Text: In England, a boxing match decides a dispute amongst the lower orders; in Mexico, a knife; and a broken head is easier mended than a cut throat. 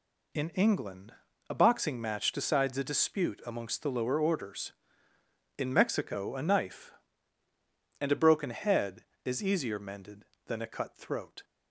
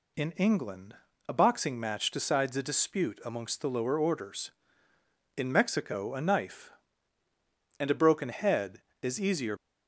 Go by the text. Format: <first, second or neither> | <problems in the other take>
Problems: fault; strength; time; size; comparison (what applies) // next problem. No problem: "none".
first | stops before "mended than a cut throat"; at 9.5 s